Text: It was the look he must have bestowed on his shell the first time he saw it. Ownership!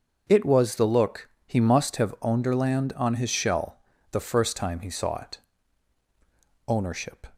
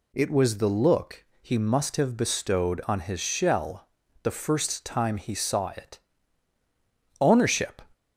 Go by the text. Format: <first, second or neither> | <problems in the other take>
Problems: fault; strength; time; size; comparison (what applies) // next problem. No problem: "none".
second | starts louder than the rest; until 1.2 s; 6.5 dB // pauses between "look" and "he"; slight; at 1.2 s; 0.18 s long; slight in the second // says "onderland" for "bestowed"; at 2.2 s // pauses between "shell" and "the"; slight; at 3.7 s; 0.34 s long; also in the second